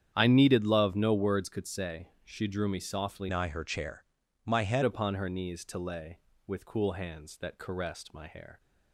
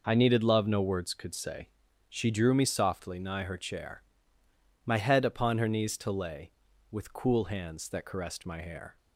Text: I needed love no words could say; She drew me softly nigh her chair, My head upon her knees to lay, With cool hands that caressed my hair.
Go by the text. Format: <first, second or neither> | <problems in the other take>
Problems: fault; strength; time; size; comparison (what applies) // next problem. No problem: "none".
second | starts louder than the rest; strong; until 1.1 s; 9 dB // changes voice from "nigh" to "head"; from 3.2 to 4.8 s; 1.6 s long